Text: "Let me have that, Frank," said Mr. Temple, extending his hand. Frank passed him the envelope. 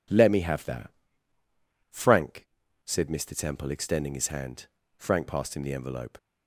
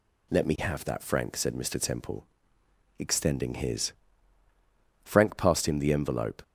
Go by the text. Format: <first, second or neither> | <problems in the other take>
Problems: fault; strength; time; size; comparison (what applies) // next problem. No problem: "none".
first | skips "hand"; at 4.4 s